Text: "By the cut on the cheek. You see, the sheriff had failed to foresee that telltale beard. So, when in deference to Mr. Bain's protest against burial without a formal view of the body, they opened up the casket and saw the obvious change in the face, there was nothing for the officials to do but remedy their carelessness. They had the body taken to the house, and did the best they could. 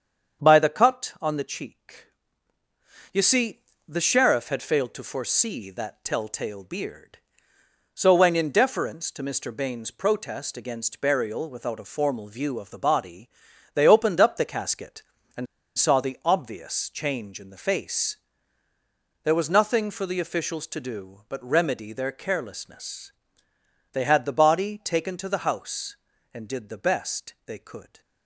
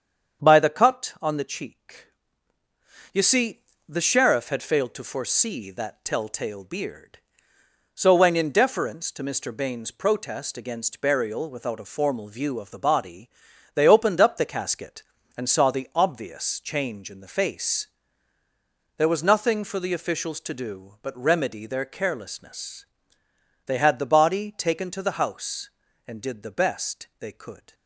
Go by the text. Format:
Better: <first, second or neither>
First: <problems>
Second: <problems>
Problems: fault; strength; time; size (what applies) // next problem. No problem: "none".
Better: second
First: starts louder than the rest; strong; until 1.5 s; 7.5 dB // pauses between "and" and "saw"; slight; at 15.4 s; 0.30 s long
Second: starts louder than the rest; strong; until 1.5 s; 7.5 dB